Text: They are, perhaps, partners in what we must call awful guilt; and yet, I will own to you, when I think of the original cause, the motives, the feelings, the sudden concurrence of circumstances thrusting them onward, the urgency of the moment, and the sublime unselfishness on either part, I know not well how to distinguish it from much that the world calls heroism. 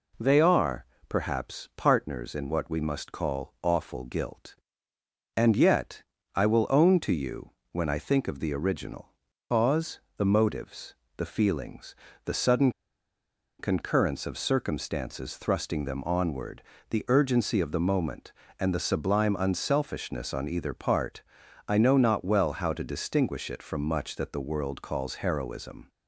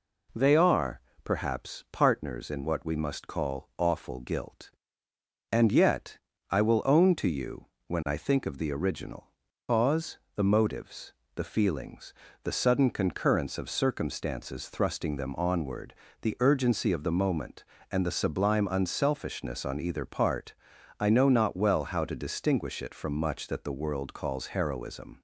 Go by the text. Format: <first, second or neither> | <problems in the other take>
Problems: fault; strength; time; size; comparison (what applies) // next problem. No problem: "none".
second | pauses between "original" and "cause"; at 9.1 s; 0.38 s long; also in the second // pauses between "sudden" and "concurrence"; noticeable; at 12.7 s; 0.89 s long